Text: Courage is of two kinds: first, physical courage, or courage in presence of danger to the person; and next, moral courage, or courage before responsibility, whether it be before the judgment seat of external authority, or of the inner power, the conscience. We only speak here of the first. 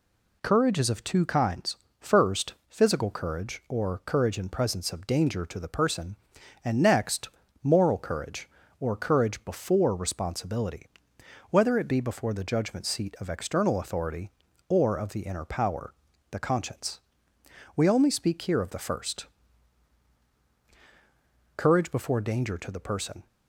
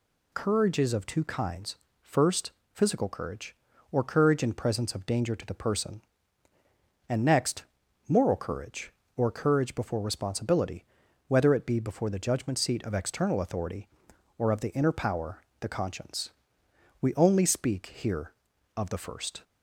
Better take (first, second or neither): second